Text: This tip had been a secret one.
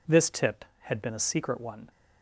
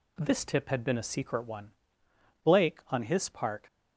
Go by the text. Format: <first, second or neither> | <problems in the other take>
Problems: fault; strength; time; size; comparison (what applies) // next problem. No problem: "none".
first | goes on to say "Blake on his part"; noticeable; from 2.4 s on; 1.1 s long